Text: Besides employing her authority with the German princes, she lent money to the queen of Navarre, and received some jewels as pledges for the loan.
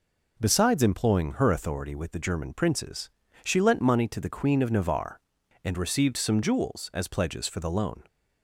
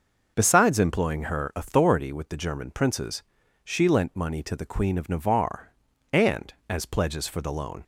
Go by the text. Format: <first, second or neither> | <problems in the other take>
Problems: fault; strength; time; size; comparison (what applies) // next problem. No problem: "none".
first | starts louder than the rest; noticeable; until 1.3 s; 6 dB // skips "received some jewels"; at 6.6 s